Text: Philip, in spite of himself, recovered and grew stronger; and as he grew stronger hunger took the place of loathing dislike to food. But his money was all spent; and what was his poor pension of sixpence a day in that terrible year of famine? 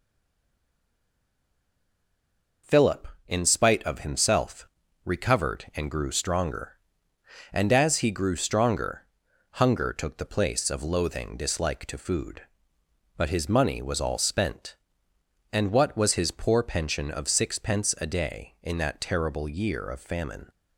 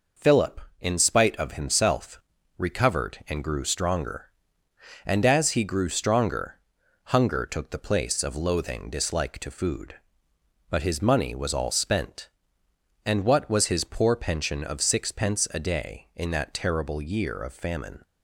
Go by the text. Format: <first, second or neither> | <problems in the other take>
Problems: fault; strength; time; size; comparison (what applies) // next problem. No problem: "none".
second | stays silent before the first word; strong; until 2.6 s; 2.6 s long // pauses between "stronger" and "hunger"; noticeable; at 9.0 s; 0.58 s long; noticeable in the second